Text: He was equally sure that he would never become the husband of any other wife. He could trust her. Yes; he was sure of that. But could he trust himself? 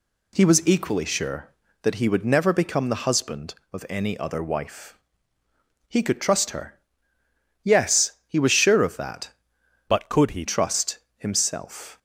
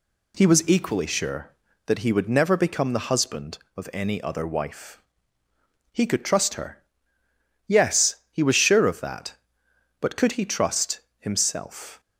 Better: second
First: changes voice from "But" to "he"; from 9.8 to 10.4 s; 0.6 s long // pauses between "trust" and "himself"; slight; at 10.9 s; 0.18 s long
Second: pauses between "trust" and "himself"; slight; at 10.9 s; 0.18 s long

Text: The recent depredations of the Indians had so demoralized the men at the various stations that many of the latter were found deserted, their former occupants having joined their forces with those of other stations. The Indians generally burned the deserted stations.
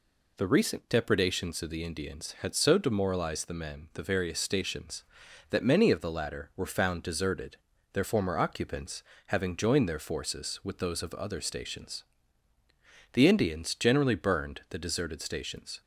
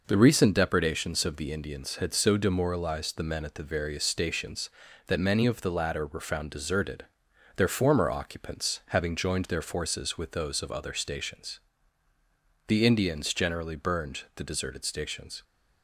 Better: second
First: skips "at"; at 3.9 s // pauses between "occupants" and "having"; slight; at 9.0 s; 0.24 s long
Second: none

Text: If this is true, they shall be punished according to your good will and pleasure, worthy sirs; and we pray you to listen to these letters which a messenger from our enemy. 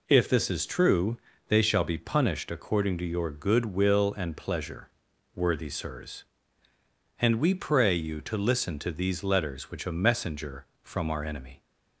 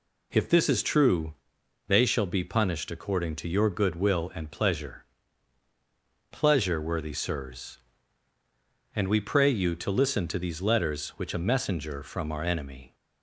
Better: first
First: none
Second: says "pleasure" twice; at 6.3 s

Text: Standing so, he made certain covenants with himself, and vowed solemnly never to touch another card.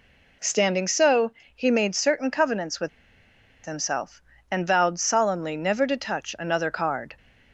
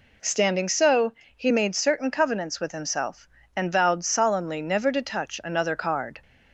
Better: second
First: pauses between "with" and "himself"; noticeable; at 2.8 s; 0.76 s long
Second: none

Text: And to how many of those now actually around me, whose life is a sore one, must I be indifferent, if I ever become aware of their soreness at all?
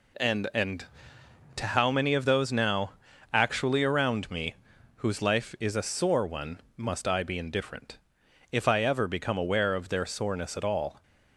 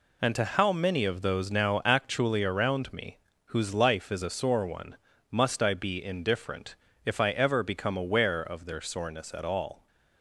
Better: second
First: says "And" twice; at 0.5 s // pauses between "now" and "actually"; at 2.9 s; 0.42 s long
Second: none

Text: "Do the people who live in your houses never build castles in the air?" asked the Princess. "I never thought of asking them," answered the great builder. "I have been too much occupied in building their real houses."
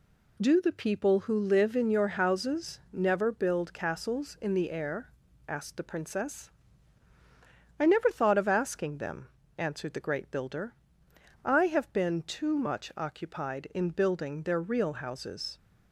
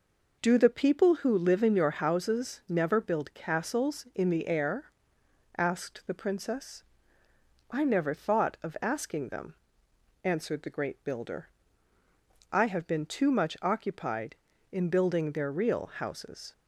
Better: neither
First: none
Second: none

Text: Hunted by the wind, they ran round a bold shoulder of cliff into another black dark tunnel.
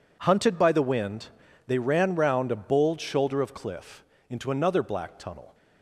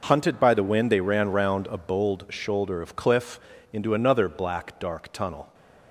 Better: second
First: pauses between "cliff" and "into"; slight; at 4.0 s; 0.24 s long // skips "dark"; at 5.1 s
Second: pauses between "cliff" and "into"; slight; at 3.3 s; 0.32 s long

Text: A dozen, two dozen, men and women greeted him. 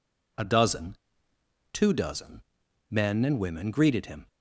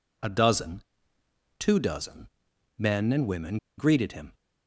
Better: first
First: none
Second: pauses between "women" and "greeted"; slight; at 3.5 s; 0.20 s long

